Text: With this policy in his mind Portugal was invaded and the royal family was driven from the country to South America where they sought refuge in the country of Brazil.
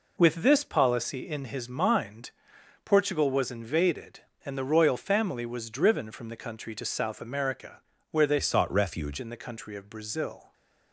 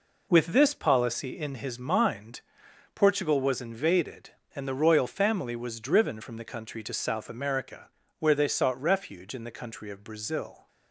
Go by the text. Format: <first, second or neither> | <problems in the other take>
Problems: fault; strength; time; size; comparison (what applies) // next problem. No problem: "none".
second | pauses between "mind" and "Portugal"; noticeable; at 2.3 s; 0.54 s long; noticeable in the second // pauses between "America" and "where"; slight; at 7.8 s; 0.30 s long; slight in the second // changes voice from "sought" to "refuge"; from 8.4 to 9.1 s; 0.7 s long